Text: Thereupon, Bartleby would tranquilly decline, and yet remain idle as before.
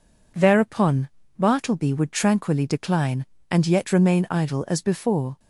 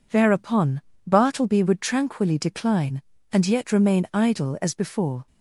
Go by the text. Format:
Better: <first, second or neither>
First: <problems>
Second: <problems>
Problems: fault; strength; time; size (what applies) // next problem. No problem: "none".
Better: neither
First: none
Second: none